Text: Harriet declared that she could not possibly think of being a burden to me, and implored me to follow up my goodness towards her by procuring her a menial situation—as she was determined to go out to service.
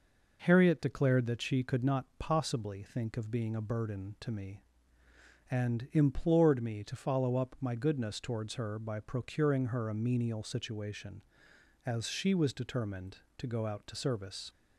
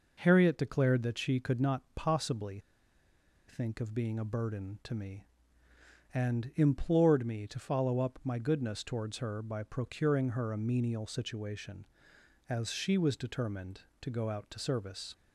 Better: first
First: none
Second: pauses between "possibly" and "think"; noticeable; at 2.5 s; 0.89 s long

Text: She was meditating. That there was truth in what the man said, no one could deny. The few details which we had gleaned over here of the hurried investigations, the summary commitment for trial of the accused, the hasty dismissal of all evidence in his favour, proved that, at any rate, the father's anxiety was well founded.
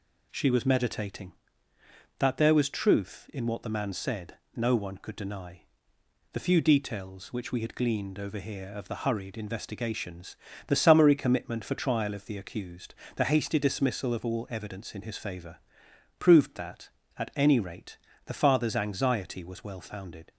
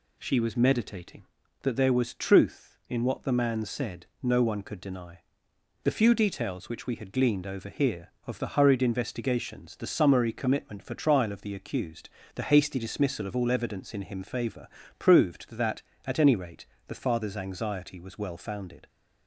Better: first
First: none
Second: says "him" for "his"; at 14.0 s

